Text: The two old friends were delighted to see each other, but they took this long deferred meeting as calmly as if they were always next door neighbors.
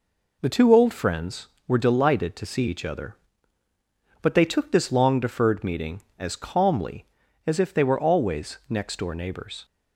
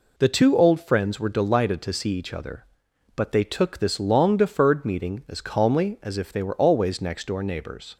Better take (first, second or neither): neither